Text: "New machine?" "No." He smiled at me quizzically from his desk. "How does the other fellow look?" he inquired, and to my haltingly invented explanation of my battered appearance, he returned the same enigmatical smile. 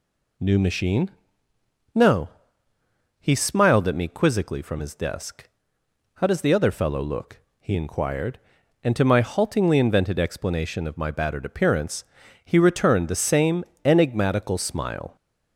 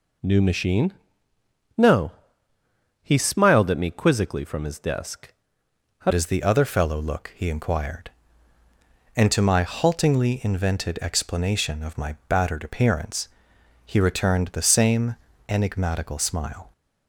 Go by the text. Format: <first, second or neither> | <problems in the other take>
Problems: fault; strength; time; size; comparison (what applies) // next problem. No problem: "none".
first | changes voice at "does"; from 6.1 s on; 10.6 s long // pauses between "same" and "enigmatical"; slight; at 15.1 s; 0.32 s long; slight in the first